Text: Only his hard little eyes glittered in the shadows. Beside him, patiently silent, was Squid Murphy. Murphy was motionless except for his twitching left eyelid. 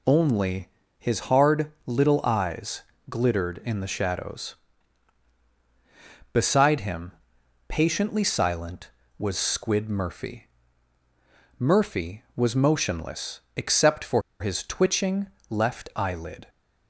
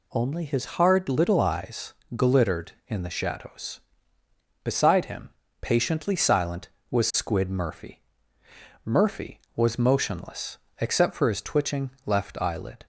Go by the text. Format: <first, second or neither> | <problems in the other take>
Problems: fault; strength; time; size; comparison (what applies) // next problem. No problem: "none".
second | pauses between "Only" and "his"; slight; at 0.6 s; 0.30 s long // pauses between "eyes" and "glittered"; slight; at 2.8 s; 0.28 s long; slight in the second // pauses between "motionless" and "except"; slight; at 13.3 s; 0.16 s long; slight in the second // pauses between "for" and "his"; slight; at 14.2 s; 0.20 s long // pauses between "twitching" and "left"; slight; at 15.2 s; 0.20 s long; slight in the second